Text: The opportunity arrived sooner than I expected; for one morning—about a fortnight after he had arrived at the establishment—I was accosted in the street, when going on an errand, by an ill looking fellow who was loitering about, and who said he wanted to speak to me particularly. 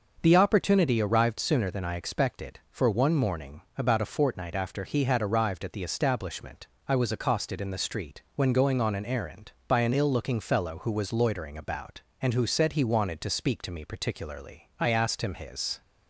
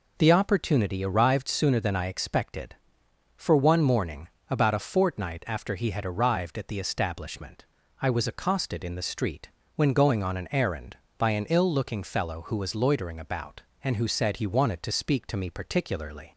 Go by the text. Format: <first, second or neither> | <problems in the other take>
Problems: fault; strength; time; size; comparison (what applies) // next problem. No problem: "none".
second | starts louder than the rest; until 1.2 s; 6 dB // goes on to say "I asked him his"; noticeable; from 14.7 s on; 1.0 s long